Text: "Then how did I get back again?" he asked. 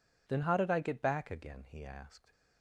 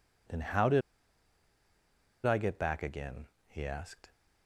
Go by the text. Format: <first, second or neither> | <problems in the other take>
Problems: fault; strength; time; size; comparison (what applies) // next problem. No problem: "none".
first | pauses between "did" and "I"; strong; at 0.8 s; 1.4 s long